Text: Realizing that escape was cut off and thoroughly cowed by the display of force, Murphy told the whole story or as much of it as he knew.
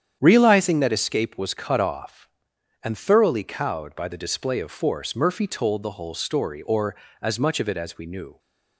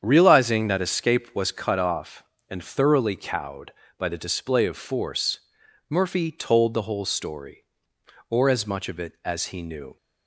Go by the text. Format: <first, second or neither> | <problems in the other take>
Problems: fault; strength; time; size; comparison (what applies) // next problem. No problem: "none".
second | starts louder than the rest; strong; until 1.2 s; 9 dB; strong in the second // says "we" for "he"; at 7.9 s